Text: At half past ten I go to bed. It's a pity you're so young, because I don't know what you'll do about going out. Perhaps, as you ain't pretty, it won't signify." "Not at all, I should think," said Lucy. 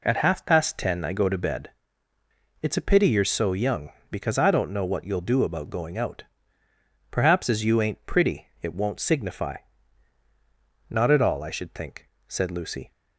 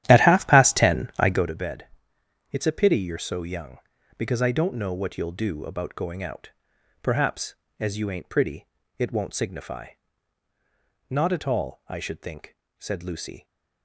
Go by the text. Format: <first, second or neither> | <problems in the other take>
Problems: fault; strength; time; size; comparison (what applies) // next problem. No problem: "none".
first | starts louder than the rest; strong; until 1.5 s; 12.5 dB